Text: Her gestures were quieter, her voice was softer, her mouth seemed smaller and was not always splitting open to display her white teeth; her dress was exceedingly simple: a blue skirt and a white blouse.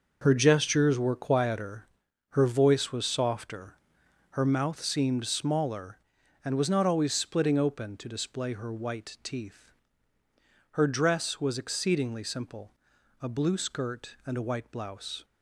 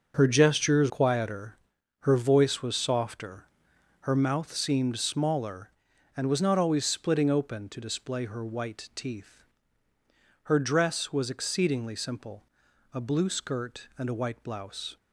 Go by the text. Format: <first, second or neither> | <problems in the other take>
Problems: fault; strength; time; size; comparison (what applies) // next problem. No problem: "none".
first | starts louder than the rest; until 1.1 s; 6.5 dB; noticeable in the first // skips "were"; at 0.8 s